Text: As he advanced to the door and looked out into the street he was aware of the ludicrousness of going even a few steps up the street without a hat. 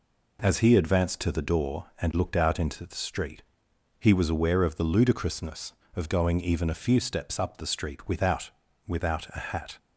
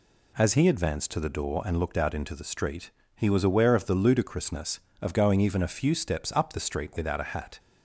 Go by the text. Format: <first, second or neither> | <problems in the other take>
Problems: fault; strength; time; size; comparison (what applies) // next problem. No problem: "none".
second | pauses between "street" and "he"; noticeable; at 3.4 s; 0.56 s long; slight in the second // says "without" twice; at 8.8 s